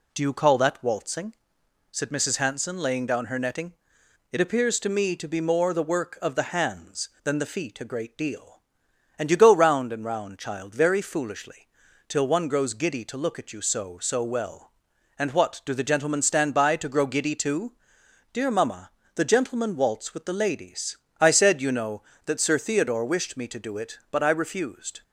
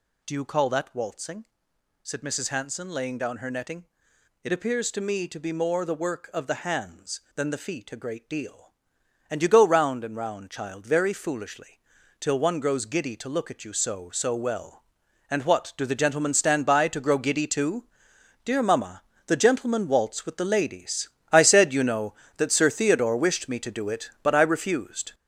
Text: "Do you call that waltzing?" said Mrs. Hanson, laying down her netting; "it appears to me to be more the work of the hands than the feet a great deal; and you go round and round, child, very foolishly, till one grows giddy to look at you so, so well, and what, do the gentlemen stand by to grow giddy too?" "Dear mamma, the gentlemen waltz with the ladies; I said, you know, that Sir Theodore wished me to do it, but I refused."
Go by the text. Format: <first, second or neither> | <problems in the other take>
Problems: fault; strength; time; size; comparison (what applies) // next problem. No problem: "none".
first | gets louder; strong; throughout; 7.5 dB